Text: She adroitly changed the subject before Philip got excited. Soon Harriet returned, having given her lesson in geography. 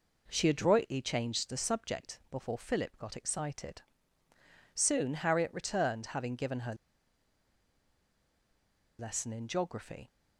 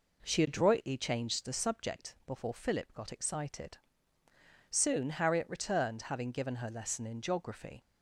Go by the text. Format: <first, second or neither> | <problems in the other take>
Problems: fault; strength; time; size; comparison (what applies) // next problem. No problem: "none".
second | pauses between "her" and "lesson"; strong; at 6.7 s; 2.2 s long